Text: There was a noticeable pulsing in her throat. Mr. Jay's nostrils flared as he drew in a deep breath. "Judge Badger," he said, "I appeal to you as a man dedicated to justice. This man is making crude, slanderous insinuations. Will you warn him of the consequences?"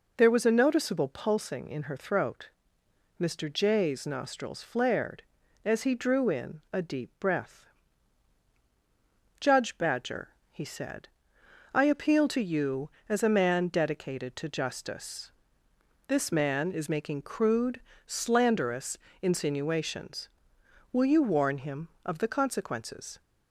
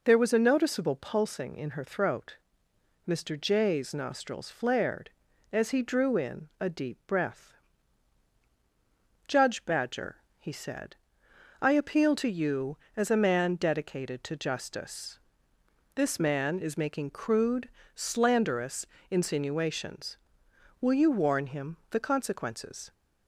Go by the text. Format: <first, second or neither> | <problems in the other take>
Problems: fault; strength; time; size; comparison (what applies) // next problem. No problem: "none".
first | pauses between "slanderous" and "insinuations"; slight; at 18.8 s; 0.26 s long; slight in the first // skips "of"; at 21.8 s